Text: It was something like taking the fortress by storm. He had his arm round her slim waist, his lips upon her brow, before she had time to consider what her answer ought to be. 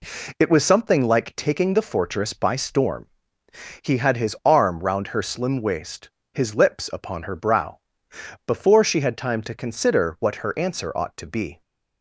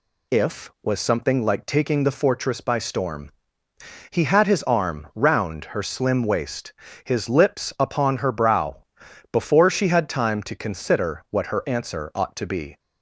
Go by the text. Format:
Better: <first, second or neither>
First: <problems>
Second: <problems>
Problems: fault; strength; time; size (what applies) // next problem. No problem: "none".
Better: first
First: none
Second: says "If" for "It"; at 0.3 s